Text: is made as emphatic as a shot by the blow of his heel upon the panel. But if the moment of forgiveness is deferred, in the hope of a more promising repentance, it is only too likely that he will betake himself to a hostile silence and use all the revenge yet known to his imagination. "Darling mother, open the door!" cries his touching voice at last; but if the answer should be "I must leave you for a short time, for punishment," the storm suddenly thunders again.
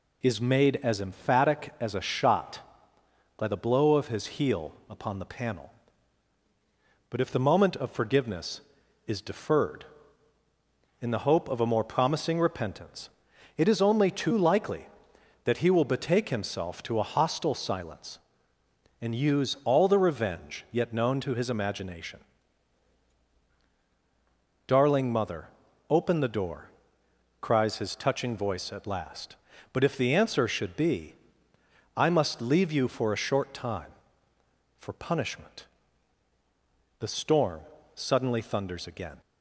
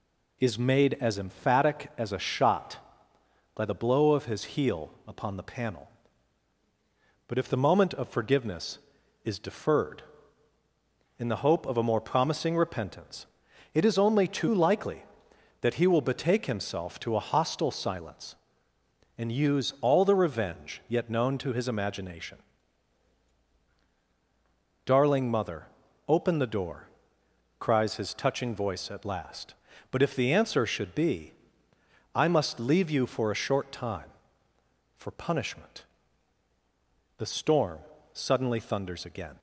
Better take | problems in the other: neither | pauses between "be" and "I"; noticeable; the same in both // pauses between "storm" and "suddenly"; slight; the same in both

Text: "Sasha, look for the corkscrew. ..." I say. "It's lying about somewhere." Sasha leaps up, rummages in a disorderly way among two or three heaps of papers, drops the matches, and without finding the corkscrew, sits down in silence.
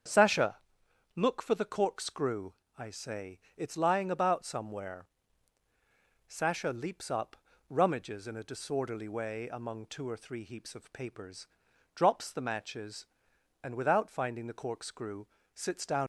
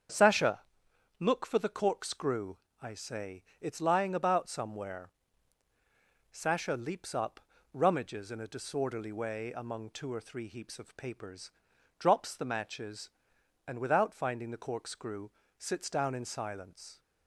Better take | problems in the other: second | starts louder than the rest; strong; until 1.6 s; 7.5 dB; strong in the second // stops before "in silence"; at 16.0 s

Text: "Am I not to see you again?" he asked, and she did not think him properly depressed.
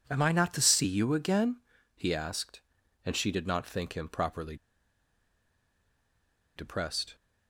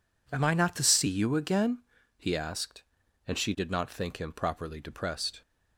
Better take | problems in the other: second | pauses between "properly" and "depressed"; strong; at 4.5 s; 2.0 s long

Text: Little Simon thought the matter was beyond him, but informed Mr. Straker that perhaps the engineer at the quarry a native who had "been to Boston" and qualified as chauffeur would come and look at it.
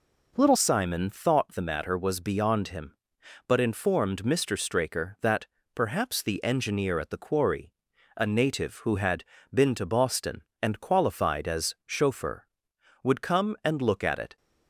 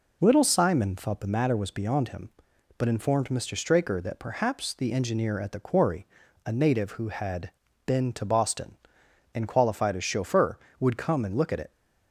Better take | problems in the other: second | changes voice at "Simon"; from 0.5 s on; 13.8 s long // pauses between "that" and "perhaps"; slight; at 5.4 s; 0.28 s long // pauses between "quarry" and "a"; at 7.7 s; 0.42 s long; also in the second // pauses between "had" and "been"; slight; at 9.2 s; 0.28 s long; slight in the second

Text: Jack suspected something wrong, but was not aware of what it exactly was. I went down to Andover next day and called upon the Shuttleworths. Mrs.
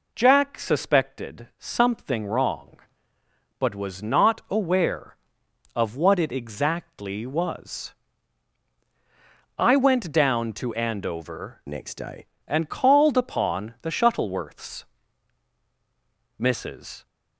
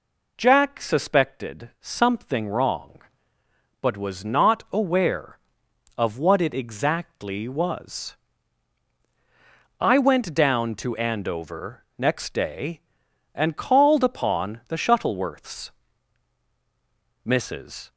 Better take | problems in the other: second | changes voice from "next" to "day"; from 11.6 to 12.2 s; 0.6 s long

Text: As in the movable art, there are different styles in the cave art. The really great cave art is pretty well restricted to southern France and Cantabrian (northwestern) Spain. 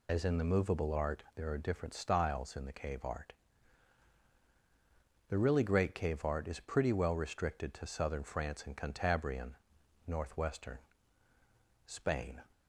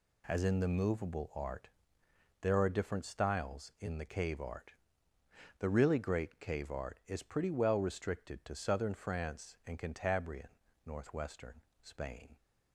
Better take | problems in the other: second | loses the start of "As"; at 0.0 s; 65 ms

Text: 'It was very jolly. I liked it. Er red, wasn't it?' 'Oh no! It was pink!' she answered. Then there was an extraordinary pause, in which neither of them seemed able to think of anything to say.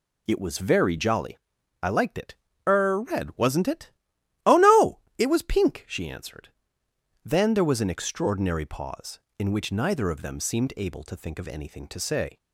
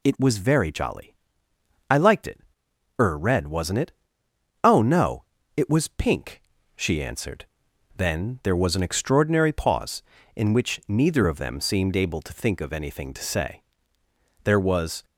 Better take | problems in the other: first | goes on to say "There was"; from 14.4 s on; 0.60 s long

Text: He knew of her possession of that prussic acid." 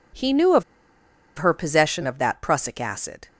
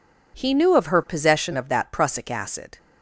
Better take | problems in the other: second | pauses between "of" and "her"; noticeable; at 0.6 s; 0.75 s long

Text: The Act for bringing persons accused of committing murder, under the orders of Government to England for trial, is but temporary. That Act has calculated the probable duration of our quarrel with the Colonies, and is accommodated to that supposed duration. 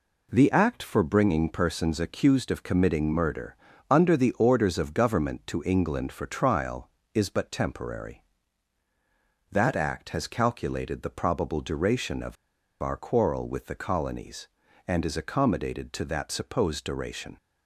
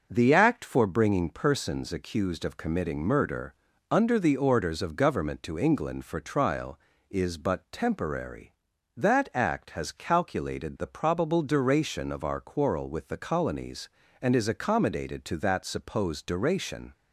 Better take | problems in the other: second | pauses between "of" and "our"; noticeable; at 12.3 s; 0.47 s long

